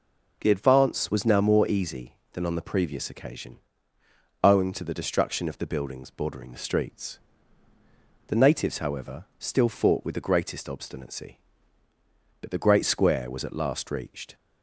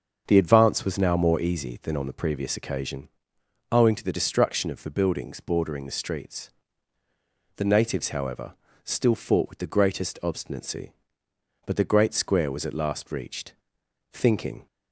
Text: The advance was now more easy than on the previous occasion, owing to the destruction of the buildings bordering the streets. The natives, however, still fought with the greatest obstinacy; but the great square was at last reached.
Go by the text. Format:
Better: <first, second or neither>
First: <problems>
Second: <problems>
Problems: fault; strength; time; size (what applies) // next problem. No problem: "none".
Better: first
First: none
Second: starts louder than the rest; until 1.2 s; 7 dB // goes on to say "Thinking"; from 14.1 s on; 0.54 s long